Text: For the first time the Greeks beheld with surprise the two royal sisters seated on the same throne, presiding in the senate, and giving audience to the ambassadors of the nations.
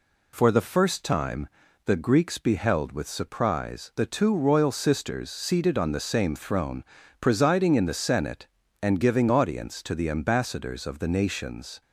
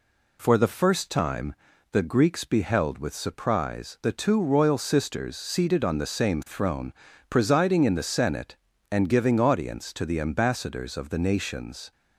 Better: neither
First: pauses between "time" and "the"; at 1.4 s; 0.38 s long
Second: pauses between "time" and "the"; at 1.5 s; 0.38 s long

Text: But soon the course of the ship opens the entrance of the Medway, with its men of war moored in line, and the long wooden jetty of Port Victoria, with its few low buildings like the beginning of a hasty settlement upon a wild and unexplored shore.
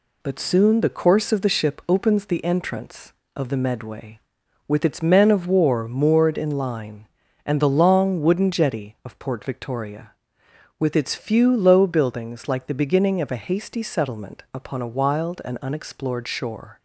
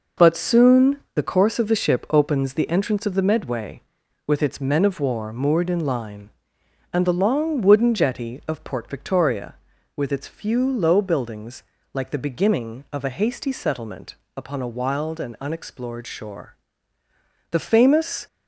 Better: first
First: none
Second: pauses between "soon" and "the"; slight; at 0.9 s; 0.16 s long // pauses between "buildings" and "like"; slight; at 11.6 s; 0.30 s long // pauses between "settlement" and "upon"; slight; at 14.1 s; 0.20 s long // goes on to say "The famous"; noticeable; from 17.5 s on; 0.76 s long

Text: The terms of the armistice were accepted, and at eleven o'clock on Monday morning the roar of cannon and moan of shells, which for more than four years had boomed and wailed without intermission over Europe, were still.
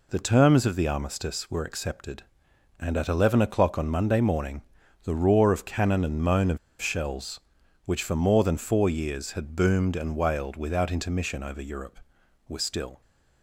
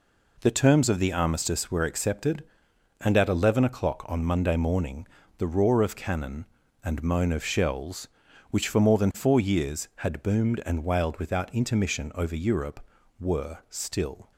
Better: second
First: pauses between "morning" and "the"; at 4.6 s; 0.42 s long // pauses between "of" and "shells"; slight; at 6.5 s; 0.22 s long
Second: pauses between "morning" and "the"; slight; at 5.0 s; 0.30 s long

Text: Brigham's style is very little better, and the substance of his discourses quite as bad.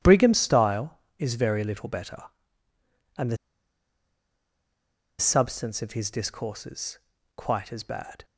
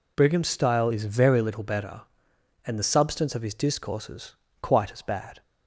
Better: second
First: pauses between "the" and "substance"; strong; at 3.3 s; 1.8 s long // pauses between "discourses" and "quite"; at 6.9 s; 0.40 s long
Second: pauses between "discourses" and "quite"; slight; at 4.3 s; 0.26 s long

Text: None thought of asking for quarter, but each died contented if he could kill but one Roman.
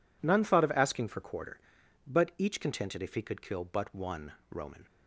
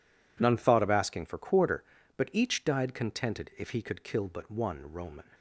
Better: second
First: skips "died"; at 2.5 s // pauses between "one" and "Roman"; slight; at 4.3 s; 0.18 s long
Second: none

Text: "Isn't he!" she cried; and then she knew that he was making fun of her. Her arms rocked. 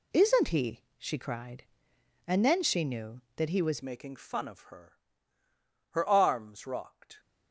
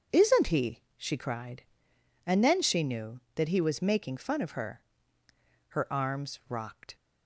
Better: second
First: changes voice at "making"; from 3.8 s on; 3.3 s long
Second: none

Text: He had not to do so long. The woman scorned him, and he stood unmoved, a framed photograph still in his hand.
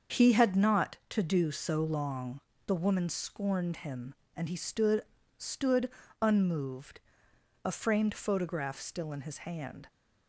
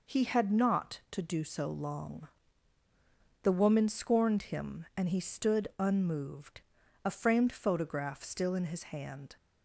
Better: second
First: starts louder than the rest; until 1.2 s; 7 dB // says "stood" twice; at 5.3 s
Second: none

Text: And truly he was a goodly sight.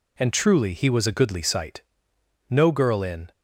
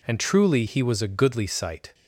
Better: second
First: goes on to say "No girl in"; noticeable; from 2.4 s on; 0.82 s long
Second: none

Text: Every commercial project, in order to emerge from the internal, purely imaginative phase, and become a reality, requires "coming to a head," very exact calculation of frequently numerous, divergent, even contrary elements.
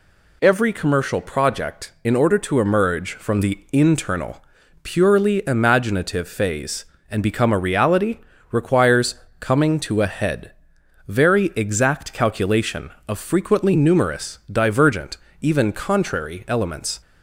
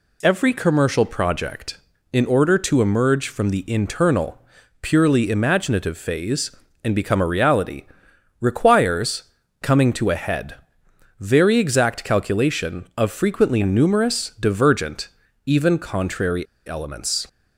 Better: first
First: pauses between "requires" and "coming"; slight; at 9.1 s; 0.24 s long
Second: pauses between "requires" and "coming"; at 9.2 s; 0.40 s long // pauses between "contrary" and "elements"; slight; at 16.4 s; 0.22 s long

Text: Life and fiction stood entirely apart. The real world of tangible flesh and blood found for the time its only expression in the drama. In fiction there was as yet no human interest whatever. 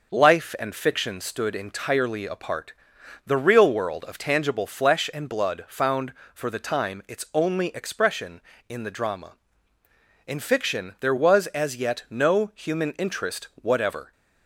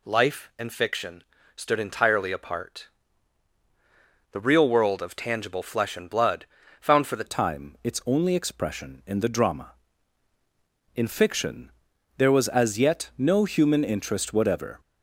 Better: first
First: none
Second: pauses between "fiction" and "stood"; slight; at 1.2 s; 0.32 s long // pauses between "blood" and "found"; slight; at 6.4 s; 0.34 s long // changes voice at "time"; from 7.2 s on; 7.5 s long // pauses between "fiction" and "there"; noticeable; at 11.7 s; 0.46 s long

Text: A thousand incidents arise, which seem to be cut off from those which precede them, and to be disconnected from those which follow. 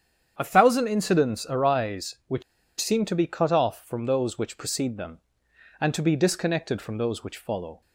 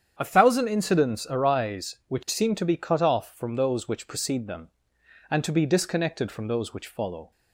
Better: second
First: starts louder than the rest; strong; until 1.4 s; 8.5 dB // pauses between "which" and "seem"; at 2.4 s; 0.37 s long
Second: starts louder than the rest; strong; until 1.2 s; 8.5 dB

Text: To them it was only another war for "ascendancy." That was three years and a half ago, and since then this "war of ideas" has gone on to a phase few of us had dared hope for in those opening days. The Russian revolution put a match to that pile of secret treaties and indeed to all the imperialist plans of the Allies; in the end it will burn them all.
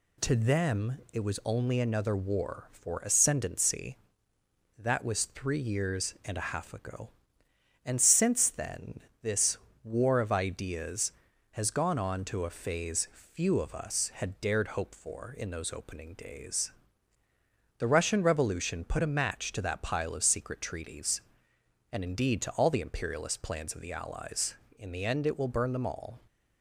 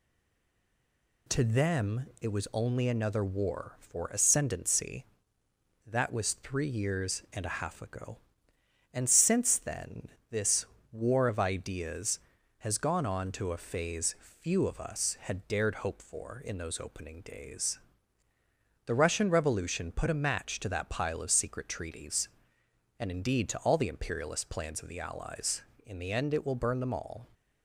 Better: first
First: pauses between "then" and "this"; slight; at 8.9 s; 0.22 s long // pauses between "this" and "war"; slight; at 9.5 s; 0.28 s long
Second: stays silent before the first word; noticeable; until 1.2 s; 1.2 s long // pauses between "then" and "this"; slight; at 10.0 s; 0.22 s long // pauses between "this" and "war"; slight; at 10.6 s; 0.28 s long

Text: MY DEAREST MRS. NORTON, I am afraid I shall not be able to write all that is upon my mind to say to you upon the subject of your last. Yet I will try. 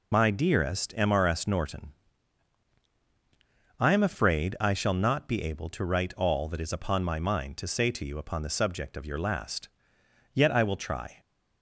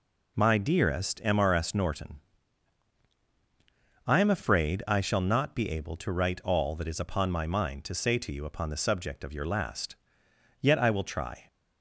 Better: second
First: loses the start of "MY"; at 0.1 s; 30 ms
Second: none

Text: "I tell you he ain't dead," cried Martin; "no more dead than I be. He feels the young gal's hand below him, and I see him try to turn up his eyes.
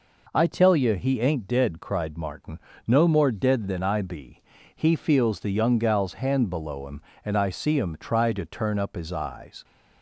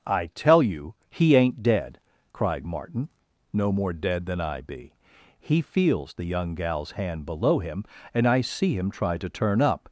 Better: first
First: none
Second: starts louder than the rest; noticeable; until 1.2 s; 6 dB // pauses between "you" and "he"; slight; at 0.9 s; 0.16 s long // stops before "his eyes"; at 9.8 s

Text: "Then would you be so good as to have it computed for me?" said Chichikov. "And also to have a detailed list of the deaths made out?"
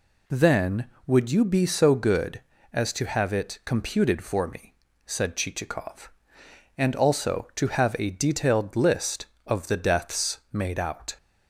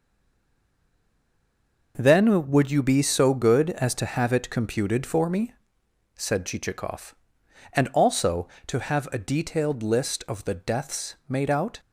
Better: first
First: none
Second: stays silent before the first word; noticeable; until 1.9 s; 1.9 s long

